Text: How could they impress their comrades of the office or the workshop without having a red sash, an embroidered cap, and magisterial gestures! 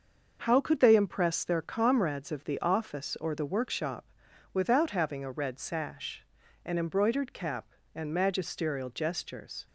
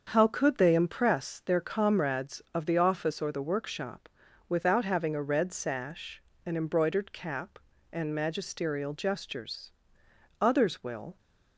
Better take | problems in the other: first | starts louder than the rest; until 1.1 s; 7 dB; also in the first // pauses between "workshop" and "without"; at 4.0 s; 0.40 s long; noticeable in the first // goes on to say "Others will"; noticeable; from 10.3 s on; 0.78 s long

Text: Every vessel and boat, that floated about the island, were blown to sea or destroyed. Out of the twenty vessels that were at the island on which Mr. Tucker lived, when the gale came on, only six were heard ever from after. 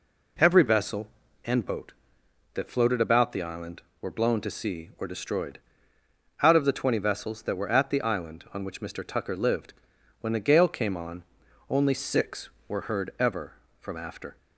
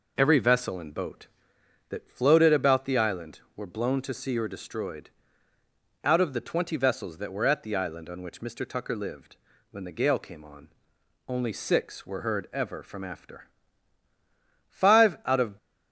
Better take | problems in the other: first | goes on to say "Five out of"; noticeable; from 14.7 s on; 0.86 s long

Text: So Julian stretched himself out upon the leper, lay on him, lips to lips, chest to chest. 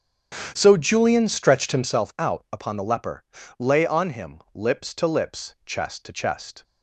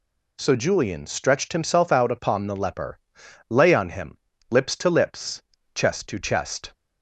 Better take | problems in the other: second | starts louder than the rest; strong; until 2.0 s; 9 dB

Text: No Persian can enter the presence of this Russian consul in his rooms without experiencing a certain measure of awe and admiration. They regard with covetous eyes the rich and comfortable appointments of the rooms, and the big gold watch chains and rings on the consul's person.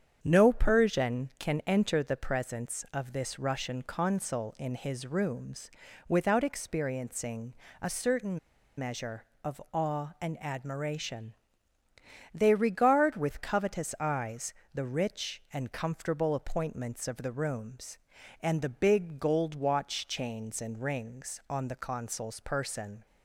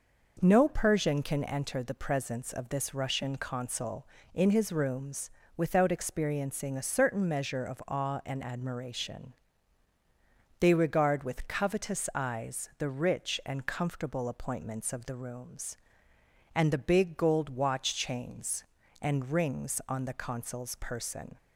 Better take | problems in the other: second | starts louder than the rest; strong; until 1.2 s; 8 dB // pauses between "rooms" and "without"; slight; at 5.7 s; 0.36 s long; slight in the second // pauses between "experiencing" and "a"; slight; at 7.5 s; 0.26 s long // pauses between "certain" and "measure"; at 8.3 s; 0.38 s long // pauses between "eyes" and "the"; slight; at 14.5 s; 0.22 s long

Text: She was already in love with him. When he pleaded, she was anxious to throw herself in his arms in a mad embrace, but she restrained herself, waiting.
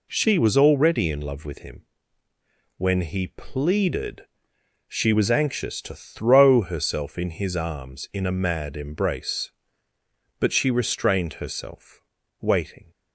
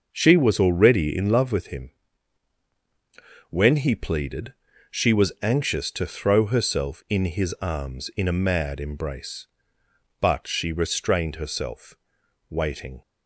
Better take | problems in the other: neither | none

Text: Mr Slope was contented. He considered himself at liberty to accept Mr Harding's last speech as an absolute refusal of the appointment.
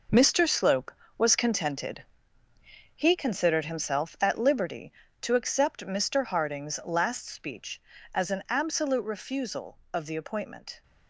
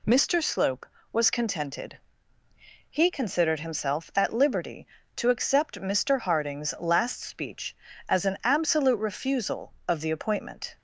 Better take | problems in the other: second | gets quieter; strong; throughout; 11.5 dB

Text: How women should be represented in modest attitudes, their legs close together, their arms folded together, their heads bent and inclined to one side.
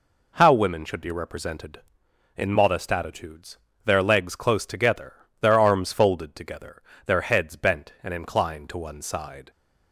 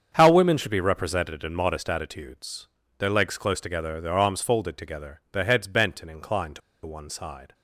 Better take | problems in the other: first | starts louder than the rest; strong; until 1.1 s; 7 dB // pauses between "to" and "one"; slight; at 6.6 s; 0.25 s long

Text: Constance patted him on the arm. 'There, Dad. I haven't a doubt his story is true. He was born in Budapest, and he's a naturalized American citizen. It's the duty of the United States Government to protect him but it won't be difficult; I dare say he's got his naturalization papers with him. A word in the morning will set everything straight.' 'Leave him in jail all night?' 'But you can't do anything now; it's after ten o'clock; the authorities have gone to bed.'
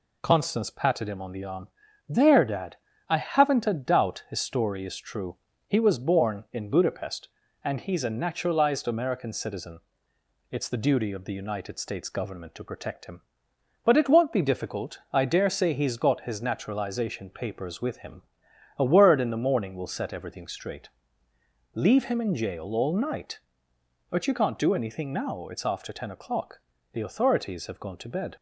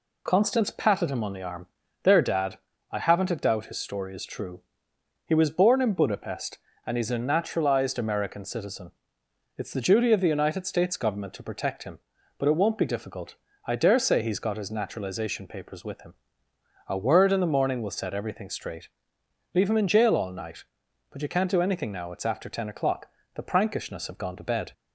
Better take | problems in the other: first | says "prankishness" for "authorities"; at 23.4 s

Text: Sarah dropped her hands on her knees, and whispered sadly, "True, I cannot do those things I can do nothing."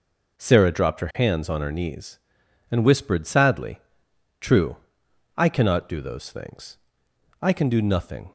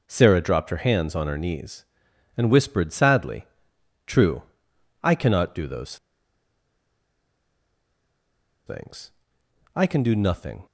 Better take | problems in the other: first | pauses between "those" and "things"; strong; at 5.9 s; 2.7 s long // pauses between "things" and "I"; noticeable; at 9.1 s; 0.64 s long; noticeable in the first

